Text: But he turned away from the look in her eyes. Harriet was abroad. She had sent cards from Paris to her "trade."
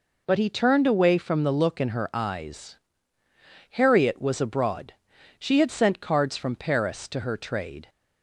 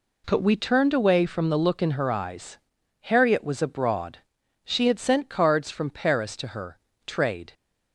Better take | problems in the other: first | says "we" for "he"; at 0.4 s // pauses between "her" and "trade"; slight; at 6.7 s; 0.26 s long

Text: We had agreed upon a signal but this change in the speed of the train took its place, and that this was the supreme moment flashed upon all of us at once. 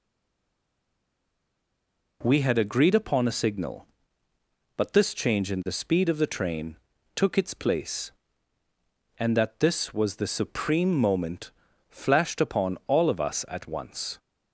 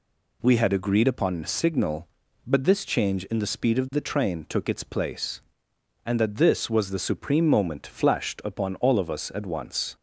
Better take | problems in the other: second | stays silent before the first word; until 2.2 s; 2.2 s long // pauses between "train" and "took"; at 6.7 s; 0.38 s long // pauses between "moment" and "flashed"; slight; at 11.5 s; 0.36 s long

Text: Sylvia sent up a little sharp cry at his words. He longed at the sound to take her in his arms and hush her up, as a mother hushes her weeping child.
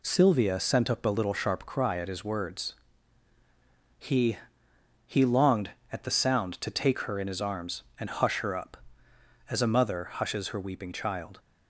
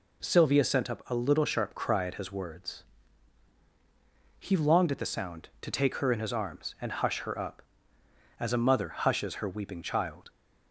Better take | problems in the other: second | says "He" twice; at 5.0 s

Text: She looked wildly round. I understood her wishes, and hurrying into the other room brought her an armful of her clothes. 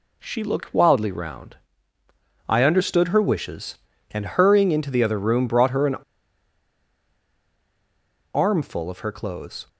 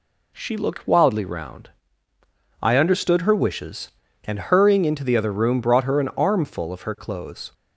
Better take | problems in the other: second | pauses between "an" and "armful"; strong; at 5.9 s; 2.3 s long

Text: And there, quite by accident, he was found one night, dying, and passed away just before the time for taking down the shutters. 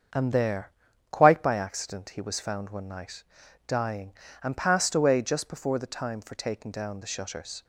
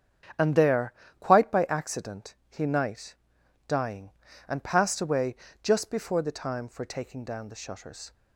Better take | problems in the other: first | starts louder than the rest; strong; until 1.6 s; 8 dB; strong in the first // skips "was found one"; at 2.6 s // pauses between "away" and "just"; slight; at 5.3 s; 0.26 s long

